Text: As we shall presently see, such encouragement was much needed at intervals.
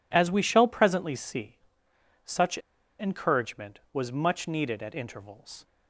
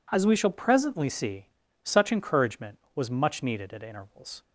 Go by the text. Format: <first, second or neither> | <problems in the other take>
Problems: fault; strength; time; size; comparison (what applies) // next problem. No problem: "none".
second | pauses between "such" and "encouragement"; at 2.5 s; 0.41 s long